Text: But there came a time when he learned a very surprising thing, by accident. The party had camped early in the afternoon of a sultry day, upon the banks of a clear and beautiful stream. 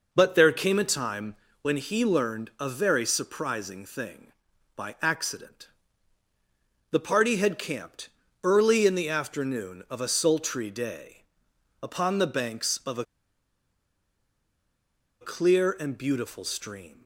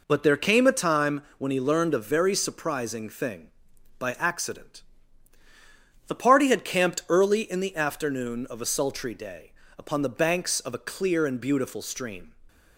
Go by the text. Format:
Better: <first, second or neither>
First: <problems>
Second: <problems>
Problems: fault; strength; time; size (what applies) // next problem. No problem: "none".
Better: second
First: pauses between "time" and "when"; slight; at 1.3 s; 0.26 s long // pauses between "camped" and "early"; slight; at 8.0 s; 0.34 s long // pauses between "a" and "clear"; strong; at 13.0 s; 2.1 s long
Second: pauses between "time" and "when"; slight; at 1.2 s; 0.16 s long